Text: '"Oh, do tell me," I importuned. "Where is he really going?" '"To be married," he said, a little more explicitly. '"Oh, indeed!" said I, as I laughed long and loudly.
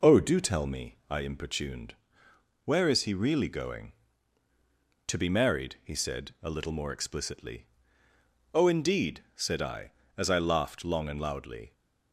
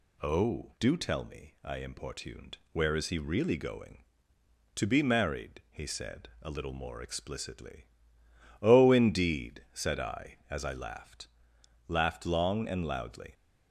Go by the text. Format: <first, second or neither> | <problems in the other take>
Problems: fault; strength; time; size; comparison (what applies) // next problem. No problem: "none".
first | says "laughed" twice; at 11.9 s